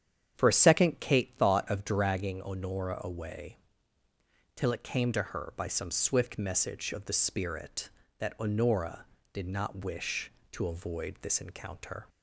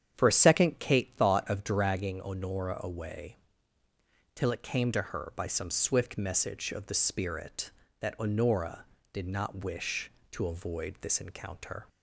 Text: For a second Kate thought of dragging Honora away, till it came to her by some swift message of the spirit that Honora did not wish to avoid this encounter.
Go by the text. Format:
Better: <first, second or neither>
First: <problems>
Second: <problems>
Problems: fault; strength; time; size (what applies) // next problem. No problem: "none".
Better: neither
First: starts louder than the rest; strong; until 1.3 s; 9 dB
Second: starts louder than the rest; strong; until 1.1 s; 9 dB